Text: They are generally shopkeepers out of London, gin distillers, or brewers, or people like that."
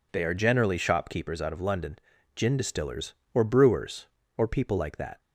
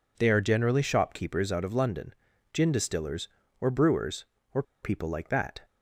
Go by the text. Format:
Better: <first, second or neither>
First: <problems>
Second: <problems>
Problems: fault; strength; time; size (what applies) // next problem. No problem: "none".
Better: first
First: none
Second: pauses between "or" and "people"; slight; at 4.6 s; 0.19 s long